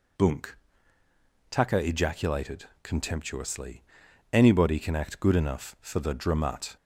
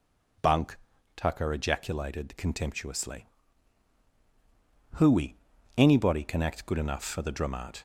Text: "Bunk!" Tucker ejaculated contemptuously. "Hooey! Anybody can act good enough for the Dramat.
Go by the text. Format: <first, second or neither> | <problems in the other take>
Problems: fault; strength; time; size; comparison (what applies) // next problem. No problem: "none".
second | pauses between "ejaculated" and "contemptuously"; slight; at 2.6 s; 0.16 s long // skips "Hooey"; at 4.0 s